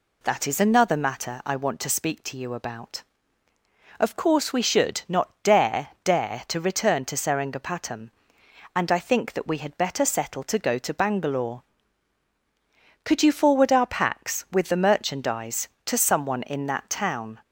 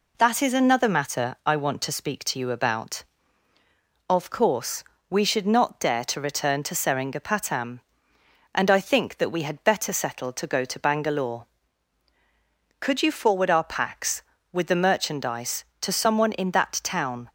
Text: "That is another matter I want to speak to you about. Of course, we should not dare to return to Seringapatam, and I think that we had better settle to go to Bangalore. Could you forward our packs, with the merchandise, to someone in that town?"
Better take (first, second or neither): second